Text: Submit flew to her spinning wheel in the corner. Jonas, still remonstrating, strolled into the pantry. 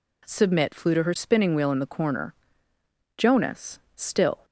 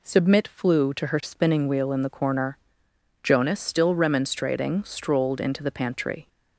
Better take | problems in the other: second | stops before "remonstrating strolled into the pantry"; at 4.4 s

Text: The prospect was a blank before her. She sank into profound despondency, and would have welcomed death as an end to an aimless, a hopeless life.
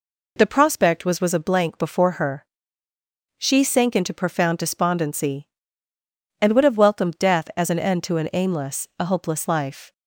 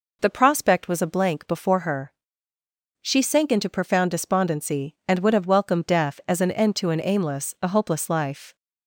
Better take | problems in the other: second | says "was" twice; at 1.1 s

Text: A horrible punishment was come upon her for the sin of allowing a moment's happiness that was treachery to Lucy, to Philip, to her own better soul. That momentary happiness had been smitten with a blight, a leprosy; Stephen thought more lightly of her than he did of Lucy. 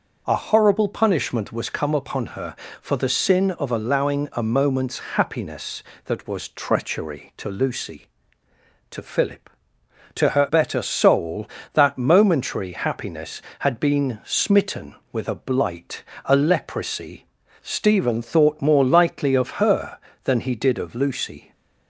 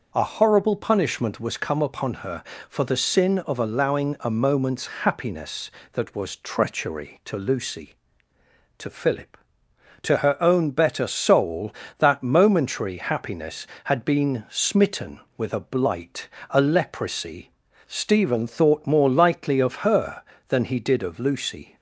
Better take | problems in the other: second | pauses between "moment's" and "happiness"; slight; at 4.9 s; 0.16 s long; slight in the second // skips "own"; at 10.4 s

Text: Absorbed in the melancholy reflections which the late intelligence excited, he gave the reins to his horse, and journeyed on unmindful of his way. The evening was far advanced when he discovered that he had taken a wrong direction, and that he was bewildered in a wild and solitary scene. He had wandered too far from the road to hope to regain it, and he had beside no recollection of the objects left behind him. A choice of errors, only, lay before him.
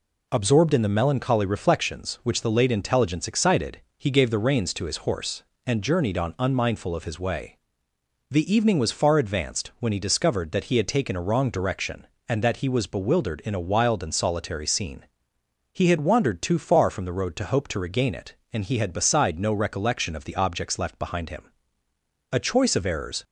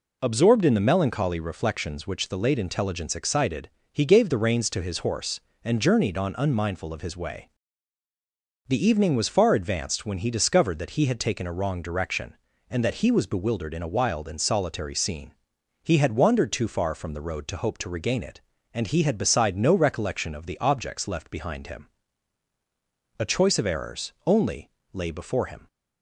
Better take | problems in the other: second | stops before "only lay before him"; at 23.2 s

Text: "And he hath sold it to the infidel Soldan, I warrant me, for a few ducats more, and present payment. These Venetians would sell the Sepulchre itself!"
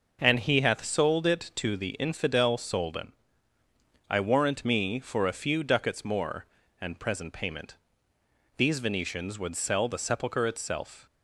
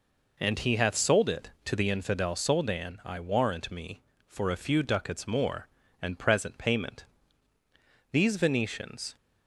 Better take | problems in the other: first | stops before "would sell the Sepulchre itself"; at 9.1 s

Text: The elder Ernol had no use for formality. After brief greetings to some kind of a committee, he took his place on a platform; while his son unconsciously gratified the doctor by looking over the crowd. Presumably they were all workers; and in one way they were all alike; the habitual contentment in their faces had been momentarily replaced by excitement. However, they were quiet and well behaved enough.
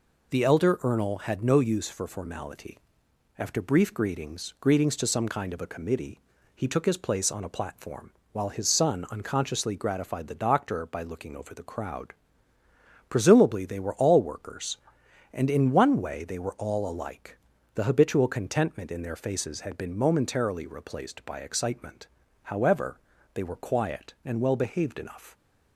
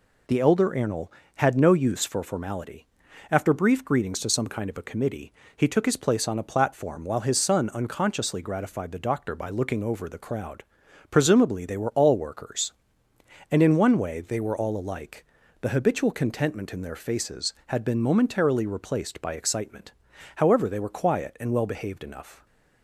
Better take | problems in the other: second | says "greetings" twice; at 4.5 s

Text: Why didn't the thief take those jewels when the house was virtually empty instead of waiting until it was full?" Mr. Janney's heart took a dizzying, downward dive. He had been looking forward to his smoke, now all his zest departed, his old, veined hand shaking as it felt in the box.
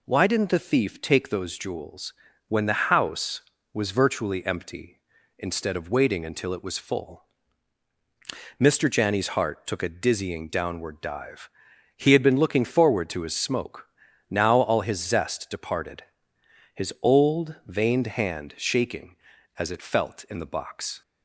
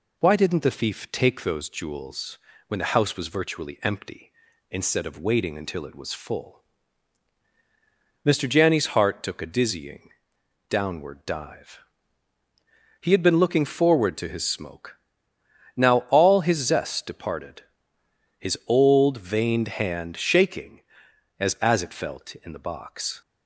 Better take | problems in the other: first | pauses between "jewels" and "when"; slight; at 2.3 s; 0.30 s long; slight in the first // says "as" twice; at 21.6 s

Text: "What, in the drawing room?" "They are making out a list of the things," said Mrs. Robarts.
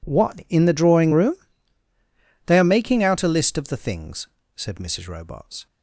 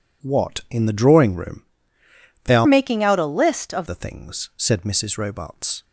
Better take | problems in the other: first | changes voice from "making" to "of"; from 2.6 to 3.8 s; 1.2 s long

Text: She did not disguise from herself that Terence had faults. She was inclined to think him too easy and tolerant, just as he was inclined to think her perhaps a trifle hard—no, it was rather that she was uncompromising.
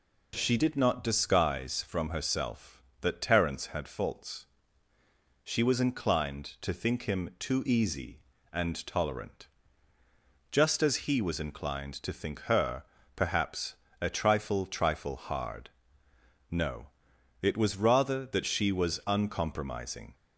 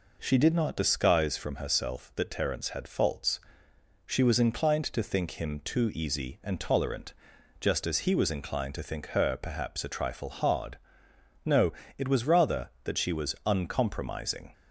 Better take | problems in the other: second | pauses between "her" and "perhaps"; slight; at 12.8 s; 0.32 s long // pauses between "perhaps" and "a"; slight; at 13.7 s; 0.24 s long // says "trifle" twice; at 14.6 s

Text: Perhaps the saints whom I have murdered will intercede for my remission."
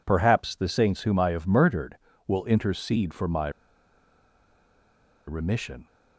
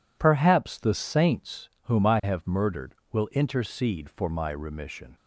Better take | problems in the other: second | pauses between "my" and "remission"; strong; at 3.4 s; 1.7 s long

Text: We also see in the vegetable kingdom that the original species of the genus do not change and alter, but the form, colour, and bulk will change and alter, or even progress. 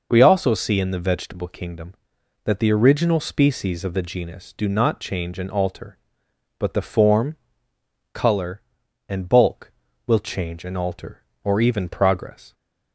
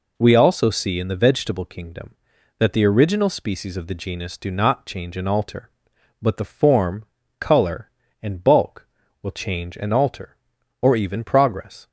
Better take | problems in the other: neither | none

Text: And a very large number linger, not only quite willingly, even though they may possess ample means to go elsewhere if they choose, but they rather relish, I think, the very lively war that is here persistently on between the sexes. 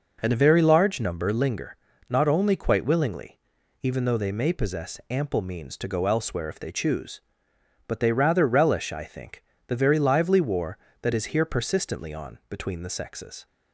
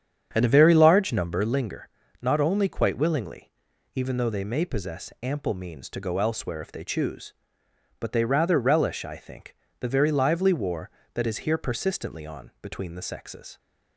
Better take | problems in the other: first | starts louder than the rest; strong; until 1.5 s; 8.5 dB

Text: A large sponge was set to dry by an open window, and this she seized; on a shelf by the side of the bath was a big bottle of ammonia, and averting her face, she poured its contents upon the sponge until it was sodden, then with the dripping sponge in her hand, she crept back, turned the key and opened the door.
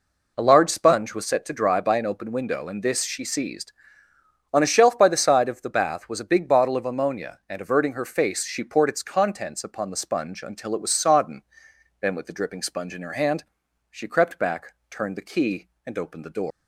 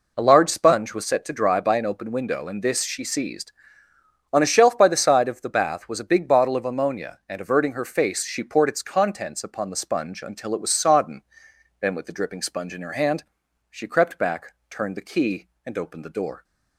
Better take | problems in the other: second | leaves "door" unfinished; at 16.5 s; 135 ms

